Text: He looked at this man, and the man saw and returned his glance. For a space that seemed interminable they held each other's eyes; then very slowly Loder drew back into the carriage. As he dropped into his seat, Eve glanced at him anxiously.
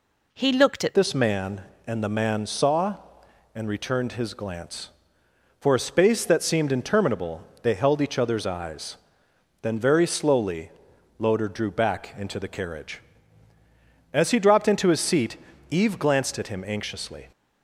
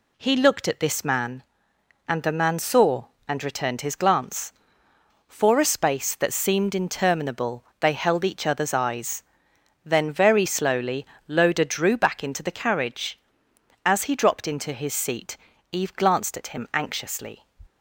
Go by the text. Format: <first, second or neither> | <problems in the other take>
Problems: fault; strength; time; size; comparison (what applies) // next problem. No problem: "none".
second | changes voice at "this"; from 0.9 s on; 16.3 s long // pauses between "interminable" and "they"; slight; at 7.4 s; 0.20 s long; slight in the second // pauses between "slowly" and "Loder"; noticeable; at 10.6 s; 0.48 s long; slight in the second